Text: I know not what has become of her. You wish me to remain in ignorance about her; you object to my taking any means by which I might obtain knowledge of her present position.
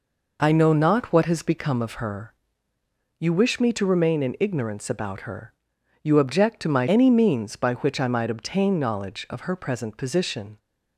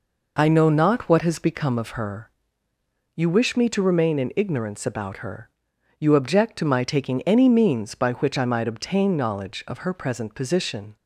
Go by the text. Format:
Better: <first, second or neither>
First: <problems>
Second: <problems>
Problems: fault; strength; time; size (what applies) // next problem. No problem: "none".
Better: second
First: skips "taking"; at 6.8 s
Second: none